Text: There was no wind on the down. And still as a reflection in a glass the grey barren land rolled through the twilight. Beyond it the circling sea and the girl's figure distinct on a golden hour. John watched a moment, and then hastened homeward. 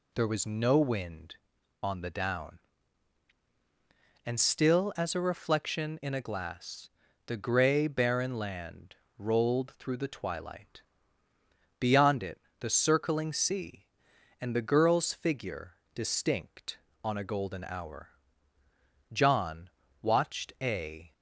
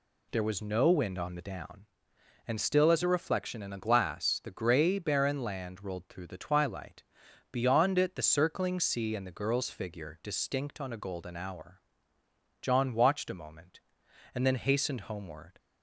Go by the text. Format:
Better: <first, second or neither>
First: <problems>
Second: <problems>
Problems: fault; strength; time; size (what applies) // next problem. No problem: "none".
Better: second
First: pauses between "glass" and "the"; at 6.8 s; 0.38 s long // pauses between "land" and "rolled"; slight; at 8.9 s; 0.20 s long // pauses between "it" and "the"; slight; at 12.4 s; 0.18 s long // pauses between "figure" and "distinct"; slight; at 15.7 s; 0.20 s long // pauses between "John" and "watched"; slight; at 19.7 s; 0.32 s long // stops before "moment and then hastened homeward"; at 21.1 s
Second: none